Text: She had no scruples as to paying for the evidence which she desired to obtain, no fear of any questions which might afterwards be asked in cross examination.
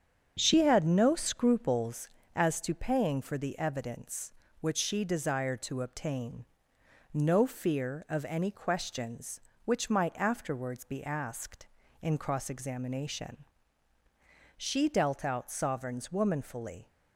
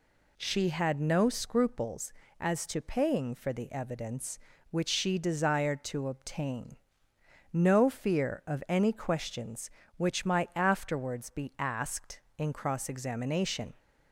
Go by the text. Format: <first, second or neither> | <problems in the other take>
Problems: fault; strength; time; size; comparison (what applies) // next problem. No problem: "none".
second | starts louder than the rest; strong; until 1.3 s; 8 dB // goes on to say "She dealt out sovereigns womanfully"; strong; from 14.5 s on; 2.3 s long